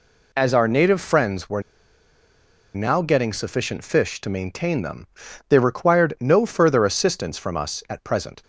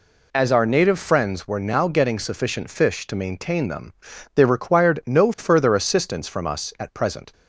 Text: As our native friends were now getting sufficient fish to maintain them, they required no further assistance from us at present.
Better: second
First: pauses between "were" and "now"; at 1.5 s; 1.1 s long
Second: none

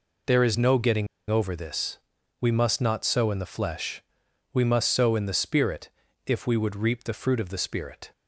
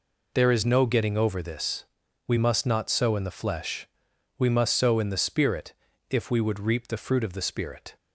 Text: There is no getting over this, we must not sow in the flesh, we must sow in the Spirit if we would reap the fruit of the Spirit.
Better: second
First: pauses between "getting" and "over"; slight; at 1.0 s; 0.23 s long // pauses between "Spirit" and "if"; slight; at 5.8 s; 0.36 s long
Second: pauses between "Spirit" and "if"; slight; at 5.7 s; 0.36 s long

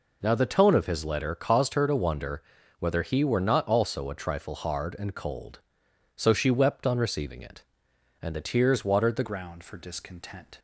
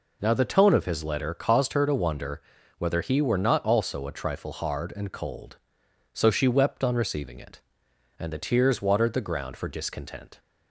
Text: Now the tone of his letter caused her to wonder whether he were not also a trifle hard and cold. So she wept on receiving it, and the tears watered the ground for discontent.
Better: second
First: pauses between "wonder" and "whether"; at 2.4 s; 0.38 s long // changes voice at "ground"; from 9.2 s on; 1.3 s long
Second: pauses between "wonder" and "whether"; at 2.4 s; 0.38 s long

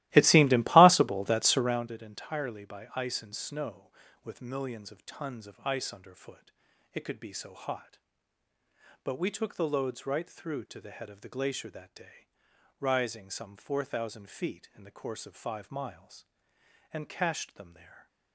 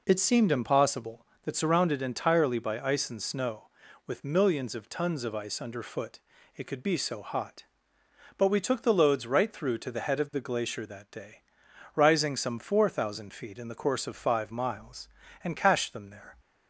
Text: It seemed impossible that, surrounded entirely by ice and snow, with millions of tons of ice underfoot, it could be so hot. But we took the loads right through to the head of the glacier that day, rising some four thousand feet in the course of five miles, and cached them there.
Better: second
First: starts louder than the rest; strong; until 1.9 s; 17.5 dB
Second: none

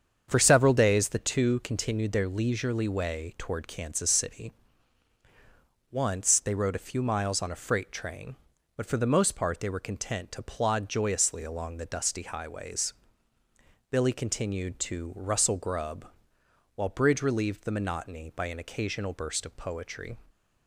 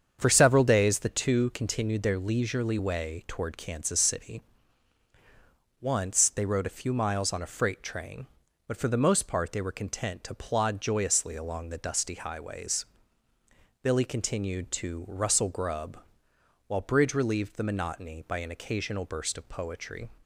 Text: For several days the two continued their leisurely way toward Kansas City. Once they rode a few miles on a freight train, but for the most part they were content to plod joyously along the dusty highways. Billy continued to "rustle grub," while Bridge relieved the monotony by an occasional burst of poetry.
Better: neither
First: starts louder than the rest; strong; until 1.3 s; 7.5 dB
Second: starts louder than the rest; strong; until 1.2 s; 7.5 dB

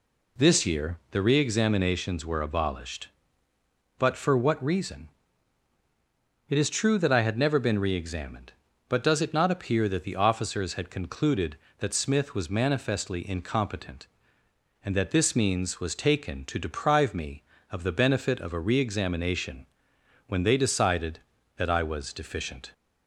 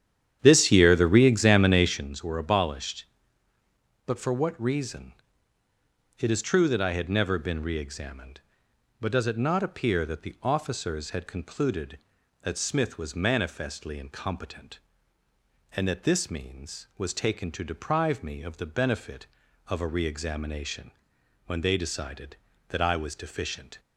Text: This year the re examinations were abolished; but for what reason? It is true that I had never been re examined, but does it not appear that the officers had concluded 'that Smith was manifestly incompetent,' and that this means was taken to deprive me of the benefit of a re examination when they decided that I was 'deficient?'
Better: first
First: pauses between "examination" and "when"; noticeable; at 19.6 s; 0.62 s long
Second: starts louder than the rest; strong; until 2.0 s; 10 dB // pauses between "examination" and "when"; noticeable; at 20.9 s; 0.56 s long

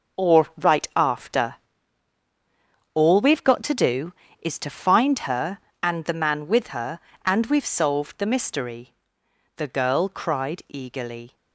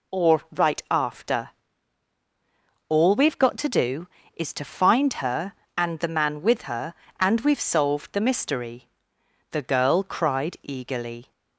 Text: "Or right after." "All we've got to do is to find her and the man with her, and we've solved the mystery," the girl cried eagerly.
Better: second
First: gets quieter; strong; throughout; 11 dB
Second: none

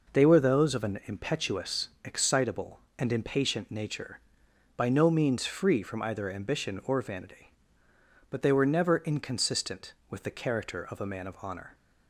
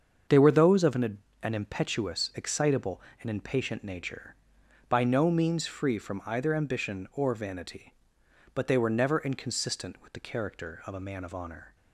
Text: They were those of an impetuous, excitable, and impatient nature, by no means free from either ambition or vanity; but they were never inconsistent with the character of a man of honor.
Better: first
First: none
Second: starts louder than the rest; until 1.4 s; 7 dB // says "an" twice; at 1.4 s

